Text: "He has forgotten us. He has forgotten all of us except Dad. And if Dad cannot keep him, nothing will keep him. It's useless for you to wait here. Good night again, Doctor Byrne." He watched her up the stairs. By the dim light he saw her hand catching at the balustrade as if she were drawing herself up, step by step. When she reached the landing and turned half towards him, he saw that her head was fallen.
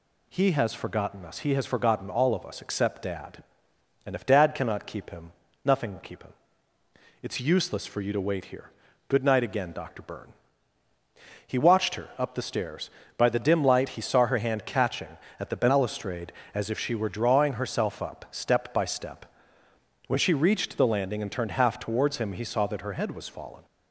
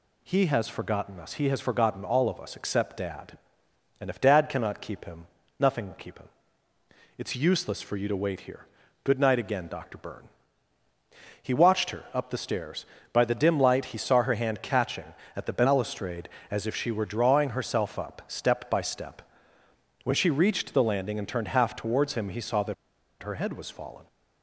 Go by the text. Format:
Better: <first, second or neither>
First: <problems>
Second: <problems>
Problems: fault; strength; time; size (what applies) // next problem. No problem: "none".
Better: first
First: none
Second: pauses between "that" and "her"; noticeable; at 22.7 s; 0.48 s long